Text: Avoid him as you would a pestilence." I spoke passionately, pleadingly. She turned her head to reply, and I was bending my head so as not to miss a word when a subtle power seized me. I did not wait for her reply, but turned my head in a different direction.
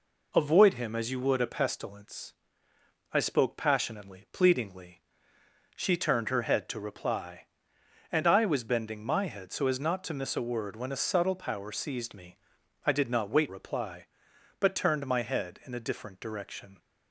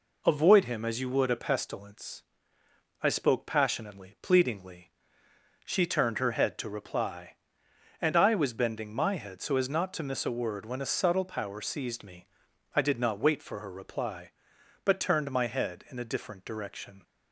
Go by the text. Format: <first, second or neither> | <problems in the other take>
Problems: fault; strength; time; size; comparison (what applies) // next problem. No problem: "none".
second | skips "for her"; at 13.4 s